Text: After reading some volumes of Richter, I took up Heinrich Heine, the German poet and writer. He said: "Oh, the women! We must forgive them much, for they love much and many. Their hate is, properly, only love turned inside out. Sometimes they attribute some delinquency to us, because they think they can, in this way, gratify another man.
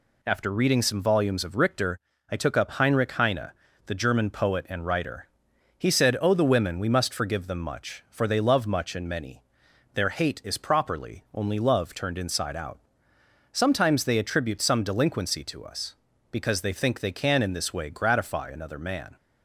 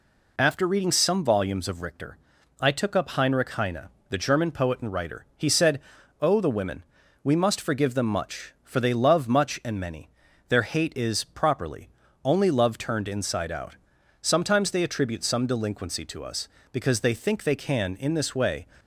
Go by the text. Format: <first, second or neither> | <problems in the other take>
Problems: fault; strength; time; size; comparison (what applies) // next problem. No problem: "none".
first | stops before "gratify another man"; at 18.7 s